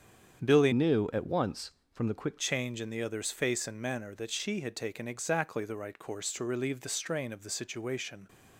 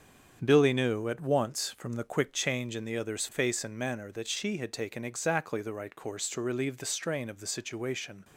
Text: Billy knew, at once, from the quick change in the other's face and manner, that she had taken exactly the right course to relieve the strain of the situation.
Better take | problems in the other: second | starts louder than the rest; strong; until 1.4 s; 8 dB; strong in the second // changes voice from "knew" to "quick"; from 0.7 to 2.3 s; 1.6 s long

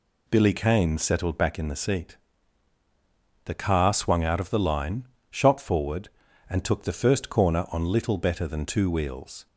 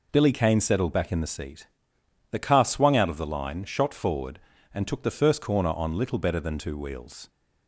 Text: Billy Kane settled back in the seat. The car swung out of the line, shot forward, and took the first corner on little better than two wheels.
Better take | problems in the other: neither | none

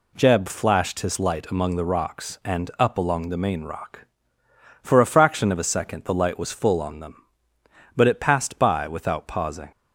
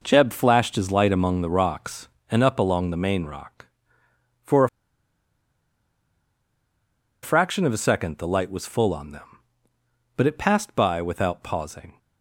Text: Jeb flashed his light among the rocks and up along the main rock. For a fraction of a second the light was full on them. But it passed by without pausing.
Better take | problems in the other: first | pauses between "a" and "fraction"; strong; at 4.6 s; 2.5 s long

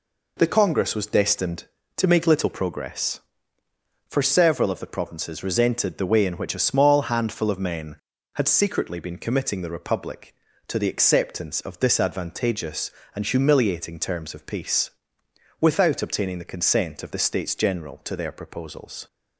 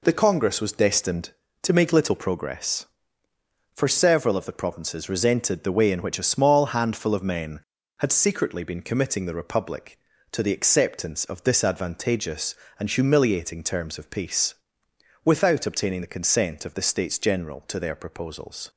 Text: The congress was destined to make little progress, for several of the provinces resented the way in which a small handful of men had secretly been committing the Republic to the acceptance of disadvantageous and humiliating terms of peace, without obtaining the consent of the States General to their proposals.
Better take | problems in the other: neither | none

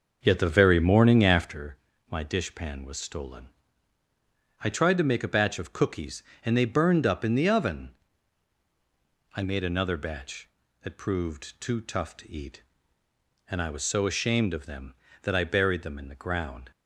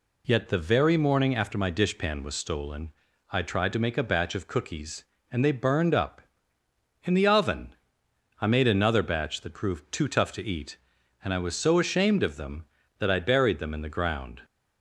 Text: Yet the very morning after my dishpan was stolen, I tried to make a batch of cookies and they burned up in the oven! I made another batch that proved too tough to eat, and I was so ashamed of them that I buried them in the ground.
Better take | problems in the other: second | starts louder than the rest; until 1.6 s; 6 dB // pauses between "after" and "my"; slight; at 1.7 s; 0.34 s long

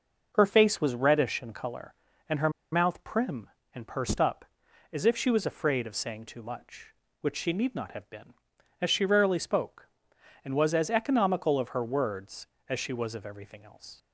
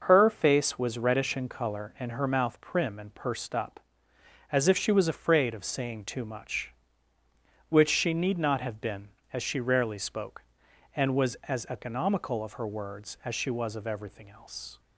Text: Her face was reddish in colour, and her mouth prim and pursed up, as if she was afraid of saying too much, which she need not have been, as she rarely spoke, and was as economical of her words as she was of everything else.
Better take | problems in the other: second | pauses between "her" and "mouth"; slight; at 2.4 s; 0.22 s long

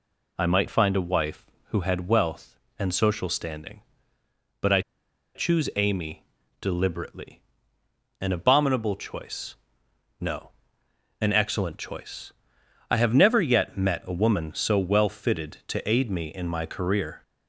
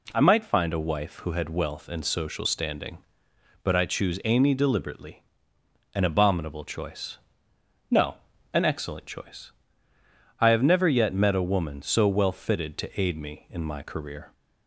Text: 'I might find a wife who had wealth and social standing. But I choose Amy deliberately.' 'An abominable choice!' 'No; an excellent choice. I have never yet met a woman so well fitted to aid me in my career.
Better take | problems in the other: second | pauses between "I" and "choose"; noticeable; at 4.7 s; 0.55 s long // pauses between "Amy" and "deliberately"; slight; at 6.2 s; 0.36 s long

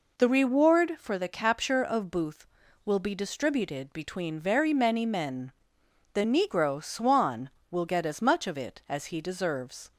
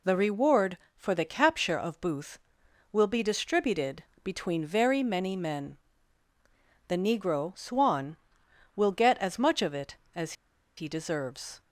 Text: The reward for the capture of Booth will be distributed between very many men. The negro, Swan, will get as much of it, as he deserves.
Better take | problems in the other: first | pauses between "distributed" and "between"; slight; at 4.0 s; 0.20 s long // pauses between "as" and "he"; at 10.3 s; 0.44 s long

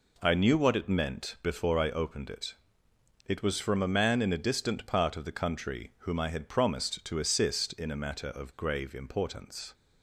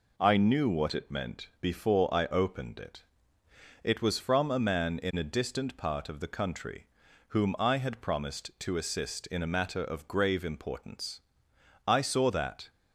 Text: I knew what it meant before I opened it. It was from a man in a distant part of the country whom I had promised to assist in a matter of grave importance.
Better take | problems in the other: first | pauses between "country" and "whom"; at 6.8 s; 0.42 s long // goes on to say "I saw that"; noticeable; from 11.8 s on; 0.84 s long

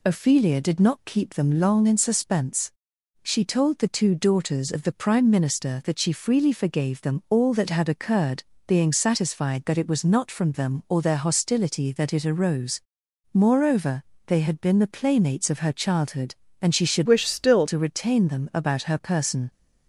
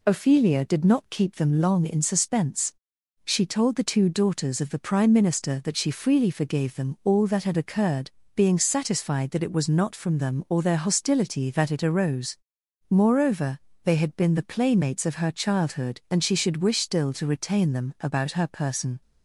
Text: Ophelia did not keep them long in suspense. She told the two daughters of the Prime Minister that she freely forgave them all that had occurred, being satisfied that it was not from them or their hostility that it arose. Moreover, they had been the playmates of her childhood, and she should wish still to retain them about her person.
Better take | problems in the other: second | changes voice from "wish" to "still"; from 17.0 to 17.6 s; 0.6 s long

